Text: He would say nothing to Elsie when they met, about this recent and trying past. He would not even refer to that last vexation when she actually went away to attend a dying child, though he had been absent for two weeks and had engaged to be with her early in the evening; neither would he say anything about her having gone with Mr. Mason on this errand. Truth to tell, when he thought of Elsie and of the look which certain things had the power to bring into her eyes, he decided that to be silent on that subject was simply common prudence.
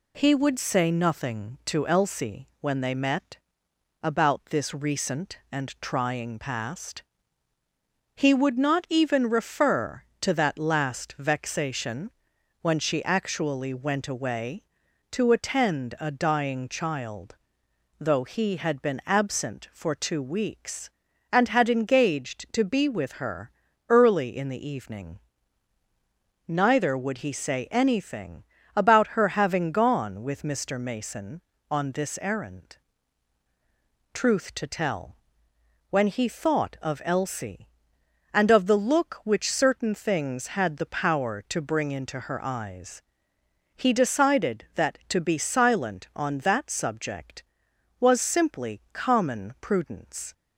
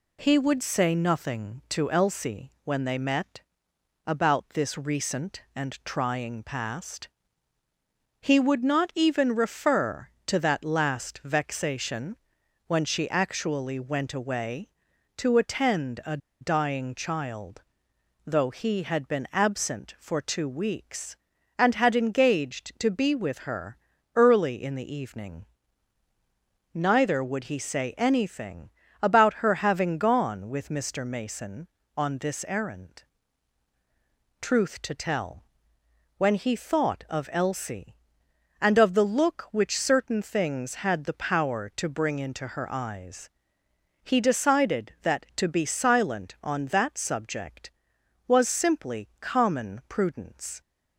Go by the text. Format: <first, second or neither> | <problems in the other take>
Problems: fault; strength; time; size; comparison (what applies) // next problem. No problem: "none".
first | pauses between "vexation" and "when"; noticeable; at 12.1 s; 0.50 s long; noticeable in the first // pauses between "a" and "dying"; slight; at 16.1 s; 0.23 s long // pauses between "her" and "early"; at 23.7 s; 0.38 s long; also in the first // pauses between "anything" and "about"; slight; at 28.7 s; 0.32 s long; slight in the first